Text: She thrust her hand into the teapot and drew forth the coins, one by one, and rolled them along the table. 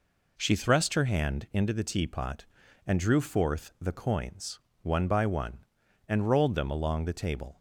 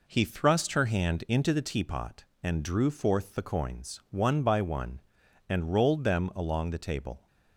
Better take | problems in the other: first | says "He" for "She"; at 0.0 s

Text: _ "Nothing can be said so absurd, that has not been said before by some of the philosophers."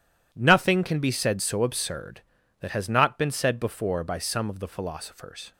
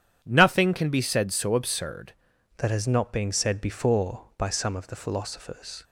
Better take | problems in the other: first | starts louder than the rest; strong; until 1.2 s; 9.5 dB // changes voice at "that"; from 2.5 s on; 3.3 s long

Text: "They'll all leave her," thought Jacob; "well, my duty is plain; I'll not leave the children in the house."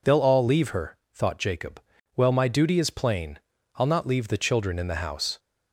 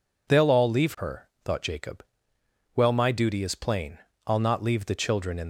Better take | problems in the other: first | stops before "the house"; at 5.4 s

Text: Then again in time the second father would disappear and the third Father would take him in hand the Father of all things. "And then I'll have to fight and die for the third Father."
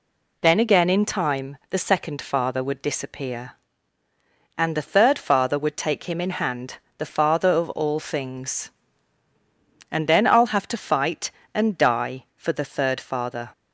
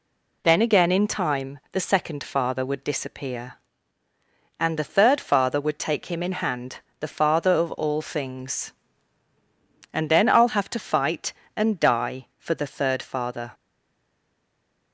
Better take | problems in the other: first | pauses between "hand" and "the"; slight; at 6.7 s; 0.20 s long; slight in the first // stays silent after the last word; noticeable; from 13.5 s on; 1.4 s long

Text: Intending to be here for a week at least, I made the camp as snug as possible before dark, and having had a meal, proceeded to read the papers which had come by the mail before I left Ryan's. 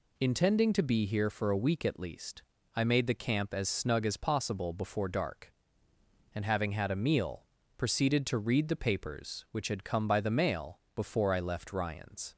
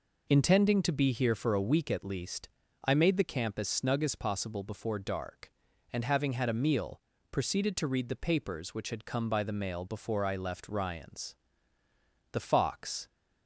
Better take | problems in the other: first | goes on to say "The Fox"; noticeable; from 12.3 s on; 0.76 s long

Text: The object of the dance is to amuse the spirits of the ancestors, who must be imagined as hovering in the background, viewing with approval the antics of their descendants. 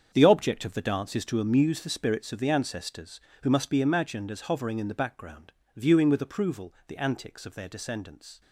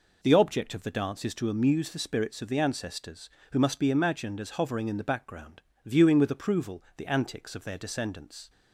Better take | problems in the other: second | gets quieter; strong; throughout; 12 dB

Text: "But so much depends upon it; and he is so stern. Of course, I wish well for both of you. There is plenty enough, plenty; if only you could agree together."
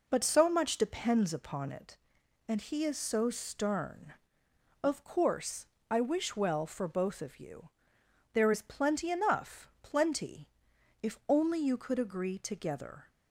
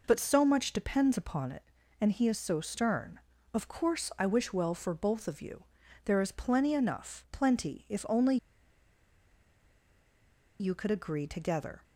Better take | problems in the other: first | pauses between "only" and "you"; strong; at 8.3 s; 2.2 s long

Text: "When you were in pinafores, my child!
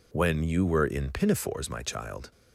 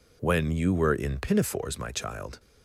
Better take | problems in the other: neither | none

